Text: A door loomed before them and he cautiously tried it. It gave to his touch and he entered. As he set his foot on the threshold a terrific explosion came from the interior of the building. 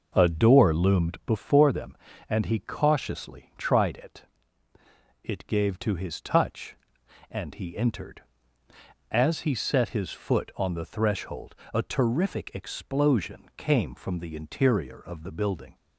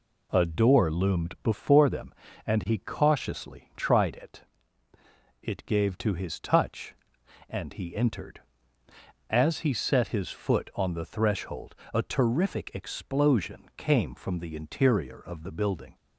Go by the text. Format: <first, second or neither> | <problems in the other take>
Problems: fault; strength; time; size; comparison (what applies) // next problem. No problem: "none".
second | starts louder than the rest; noticeable; until 1.2 s; 5.5 dB // pauses between "threshold" and "a"; slight; at 11.5 s; 0.20 s long; slight in the second